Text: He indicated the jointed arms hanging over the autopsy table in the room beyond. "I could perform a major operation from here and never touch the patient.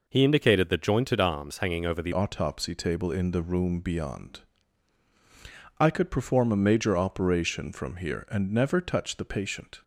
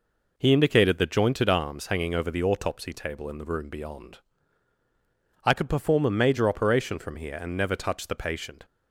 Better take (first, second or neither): second